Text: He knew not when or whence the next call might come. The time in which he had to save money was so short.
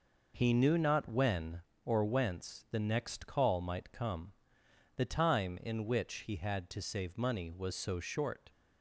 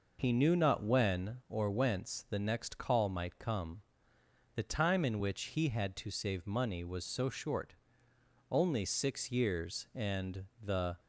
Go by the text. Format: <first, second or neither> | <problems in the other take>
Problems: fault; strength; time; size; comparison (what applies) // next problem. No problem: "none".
first | goes on to say "Only six years and the"; strong; from 8.5 s on; 2.4 s long